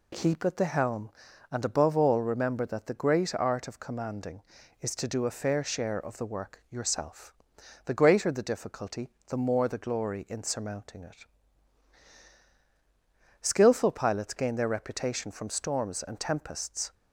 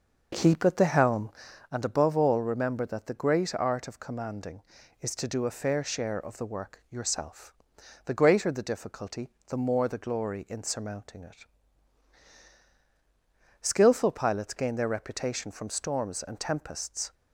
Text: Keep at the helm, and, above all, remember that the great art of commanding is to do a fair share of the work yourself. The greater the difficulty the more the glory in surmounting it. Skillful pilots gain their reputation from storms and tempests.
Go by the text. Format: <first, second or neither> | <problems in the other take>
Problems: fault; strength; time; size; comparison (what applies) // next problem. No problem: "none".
first | starts louder than the rest; noticeable; until 1.7 s; 6 dB // pauses between "difficulty" and "the"; slight; at 9.2 s; 0.18 s long; slight in the first